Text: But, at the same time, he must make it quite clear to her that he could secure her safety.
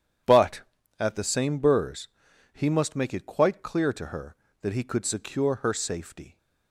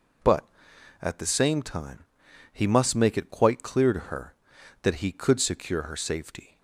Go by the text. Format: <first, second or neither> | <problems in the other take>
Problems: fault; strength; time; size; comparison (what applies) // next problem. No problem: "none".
second | says "burrs" for "time"; at 1.5 s